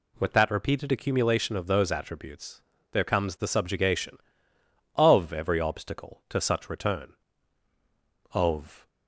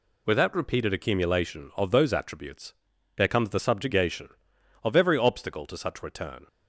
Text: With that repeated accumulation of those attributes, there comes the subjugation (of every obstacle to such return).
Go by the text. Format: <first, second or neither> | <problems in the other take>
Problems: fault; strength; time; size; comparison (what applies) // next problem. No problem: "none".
second | goes on to say "Of"; from 8.3 s on; 0.54 s long